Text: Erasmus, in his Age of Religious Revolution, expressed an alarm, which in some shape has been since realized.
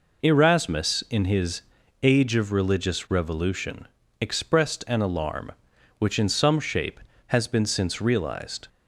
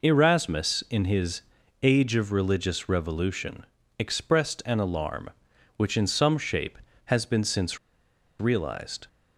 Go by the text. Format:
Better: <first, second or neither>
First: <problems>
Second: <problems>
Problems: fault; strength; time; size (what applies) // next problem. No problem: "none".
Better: first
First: pauses between "his" and "Age"; at 1.6 s; 0.42 s long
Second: pauses between "his" and "Age"; at 1.4 s; 0.42 s long // pauses between "since" and "realized"; noticeable; at 7.7 s; 0.63 s long